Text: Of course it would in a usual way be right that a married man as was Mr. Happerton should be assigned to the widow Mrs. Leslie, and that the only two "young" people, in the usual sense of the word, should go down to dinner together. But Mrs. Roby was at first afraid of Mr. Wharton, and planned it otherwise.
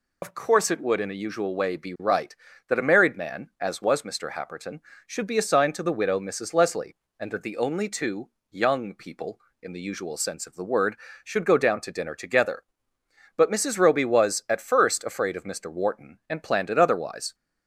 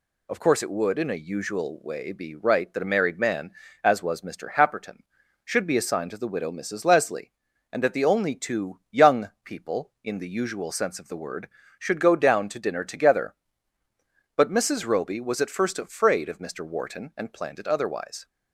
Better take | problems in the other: second | loses the start of "Of"; at 0.2 s; 50 ms // pauses between "two" and "young"; slight; at 8.2 s; 0.22 s long

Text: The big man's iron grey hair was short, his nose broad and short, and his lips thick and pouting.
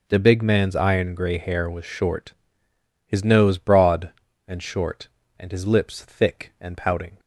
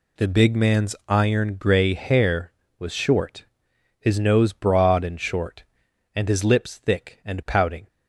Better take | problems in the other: neither | none

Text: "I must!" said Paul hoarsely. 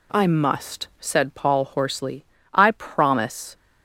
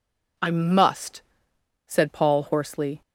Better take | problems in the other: second | goes on to say "I promise"; noticeable; from 2.5 s on; 1.0 s long

